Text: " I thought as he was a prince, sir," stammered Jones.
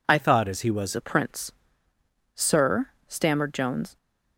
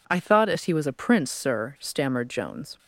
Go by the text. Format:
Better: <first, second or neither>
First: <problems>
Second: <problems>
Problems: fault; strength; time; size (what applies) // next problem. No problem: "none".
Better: second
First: changes voice from "thought" to "was"; from 0.1 to 0.9 s; 0.8 s long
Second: none